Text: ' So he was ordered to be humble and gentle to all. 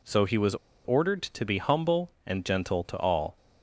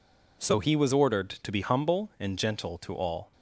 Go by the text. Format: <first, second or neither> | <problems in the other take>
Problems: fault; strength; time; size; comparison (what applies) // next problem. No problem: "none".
second | pauses between "was" and "ordered"; slight; at 0.5 s; 0.31 s long